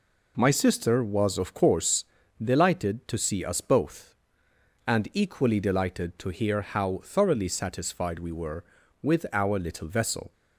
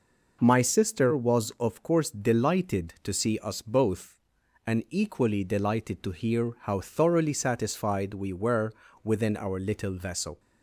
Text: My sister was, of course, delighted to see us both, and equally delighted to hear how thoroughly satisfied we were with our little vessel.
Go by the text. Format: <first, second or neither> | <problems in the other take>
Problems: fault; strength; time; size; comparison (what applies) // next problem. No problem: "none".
first | says "within" for "with"; at 9.0 s